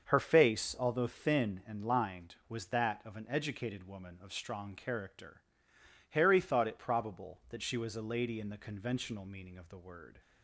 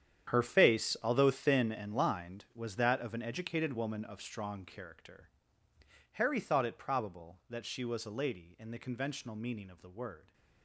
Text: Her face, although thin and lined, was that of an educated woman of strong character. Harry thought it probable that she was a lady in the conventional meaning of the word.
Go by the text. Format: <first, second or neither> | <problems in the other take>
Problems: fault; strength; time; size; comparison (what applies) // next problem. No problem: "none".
first | gets quieter; strong; throughout; 14.5 dB // starts louder than the rest; strong; until 1.3 s; 9 dB; also in the first